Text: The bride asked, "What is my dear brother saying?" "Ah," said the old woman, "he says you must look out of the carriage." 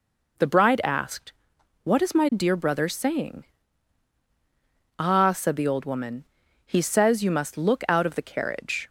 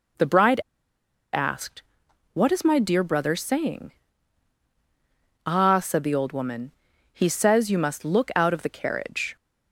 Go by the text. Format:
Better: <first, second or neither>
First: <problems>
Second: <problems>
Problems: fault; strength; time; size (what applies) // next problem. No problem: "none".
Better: first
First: none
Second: pauses between "bride" and "asked"; noticeable; at 0.6 s; 0.72 s long